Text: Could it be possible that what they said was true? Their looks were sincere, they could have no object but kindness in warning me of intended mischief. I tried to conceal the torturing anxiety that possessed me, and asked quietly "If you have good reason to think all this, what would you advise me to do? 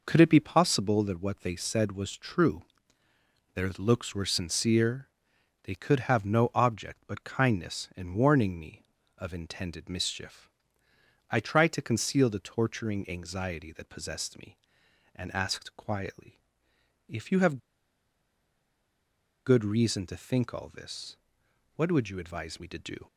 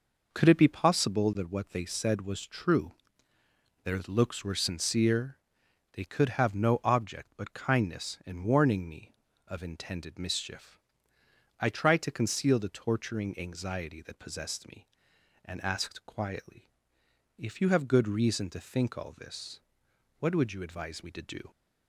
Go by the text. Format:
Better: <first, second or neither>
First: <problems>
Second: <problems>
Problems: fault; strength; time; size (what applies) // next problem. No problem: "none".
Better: second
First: pauses between "quietly" and "If"; noticeable; at 16.3 s; 0.68 s long // pauses between "have" and "good"; strong; at 17.5 s; 1.8 s long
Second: pauses between "quietly" and "If"; noticeable; at 16.6 s; 0.68 s long